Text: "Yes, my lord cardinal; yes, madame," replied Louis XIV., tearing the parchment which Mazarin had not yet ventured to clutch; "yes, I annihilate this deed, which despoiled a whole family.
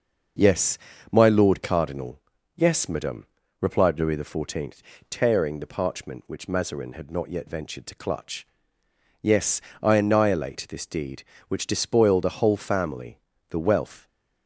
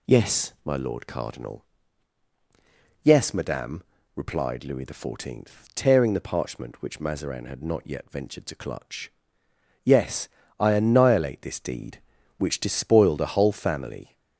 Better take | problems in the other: second | goes on to say "The wealth"; from 13.4 s on; 0.58 s long

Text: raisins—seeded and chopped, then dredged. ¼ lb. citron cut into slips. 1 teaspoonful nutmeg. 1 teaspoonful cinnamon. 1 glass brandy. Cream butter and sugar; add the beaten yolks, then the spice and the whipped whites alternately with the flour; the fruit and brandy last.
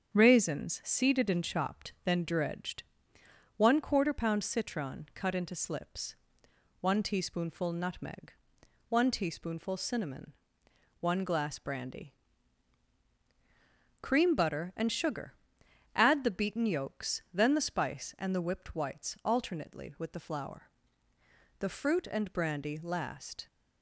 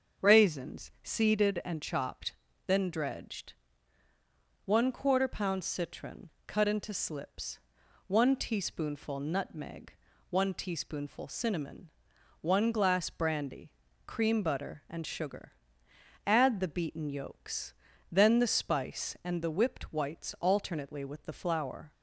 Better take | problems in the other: first | starts louder than the rest; until 1.3 s; 7 dB; strong in the first // pauses between "citron" and "cut"; slight; at 6.2 s; 0.18 s long // stops before "the fruit and brandy last"; at 21.9 s

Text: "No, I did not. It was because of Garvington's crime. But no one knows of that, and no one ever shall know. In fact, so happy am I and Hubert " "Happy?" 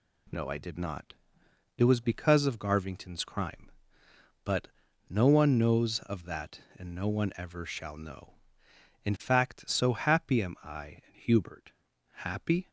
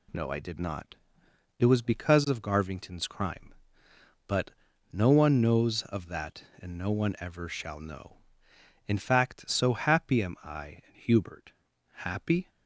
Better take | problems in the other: neither | pauses between "But" and "no"; the same in both

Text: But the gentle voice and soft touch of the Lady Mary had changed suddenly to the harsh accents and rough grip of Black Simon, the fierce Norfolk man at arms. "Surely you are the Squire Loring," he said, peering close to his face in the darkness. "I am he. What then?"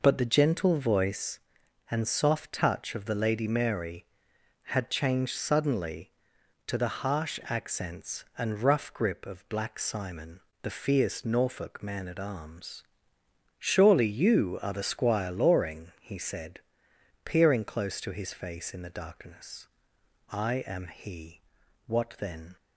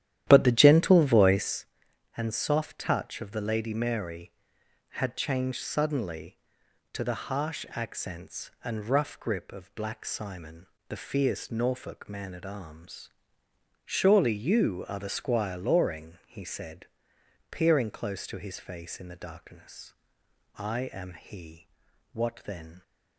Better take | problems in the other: first | starts louder than the rest; strong; until 1.7 s; 12 dB

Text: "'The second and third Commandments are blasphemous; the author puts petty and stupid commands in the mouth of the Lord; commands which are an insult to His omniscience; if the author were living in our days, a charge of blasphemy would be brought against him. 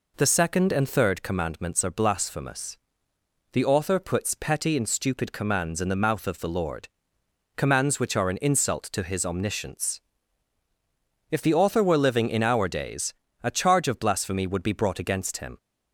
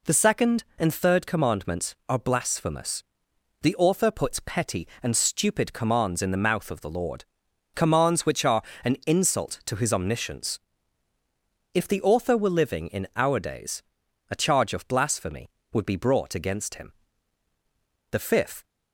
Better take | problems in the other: first | pauses between "are" and "an"; slight; at 8.6 s; 0.20 s long // goes on to say "The fifth"; from 18.0 s on; 0.54 s long

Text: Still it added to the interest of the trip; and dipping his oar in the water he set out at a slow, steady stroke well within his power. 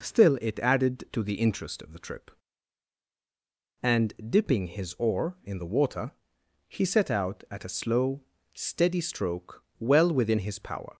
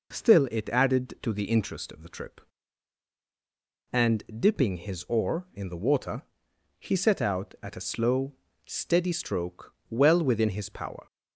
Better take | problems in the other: neither | pauses between "and" and "dipping"; slight; the same in both // pauses between "water" and "he"; noticeable; the same in both // pauses between "stroke" and "well"; slight; the same in both

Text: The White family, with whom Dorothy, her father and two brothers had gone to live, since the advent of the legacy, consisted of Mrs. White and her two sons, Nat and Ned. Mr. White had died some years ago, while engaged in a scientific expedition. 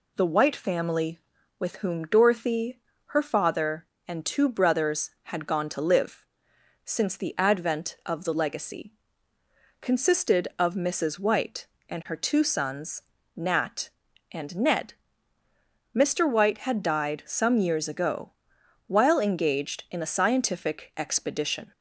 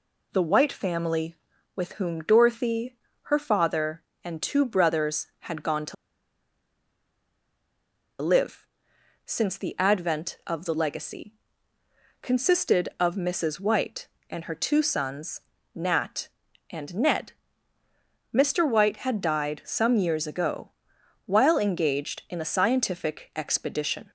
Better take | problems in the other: first | pauses between "to" and "live"; strong; at 5.9 s; 2.2 s long

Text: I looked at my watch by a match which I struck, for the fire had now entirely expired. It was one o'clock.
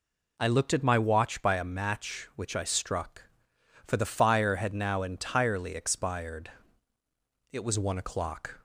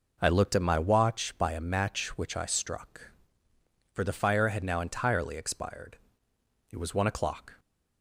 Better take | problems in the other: neither | none

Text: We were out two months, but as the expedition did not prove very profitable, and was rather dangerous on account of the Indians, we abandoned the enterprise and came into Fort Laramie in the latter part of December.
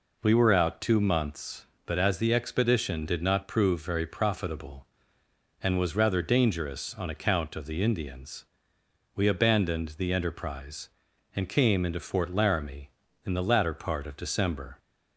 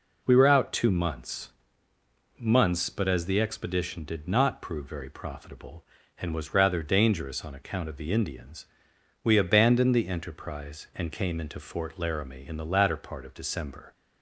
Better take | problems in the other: first | says "months" twice; at 2.3 s

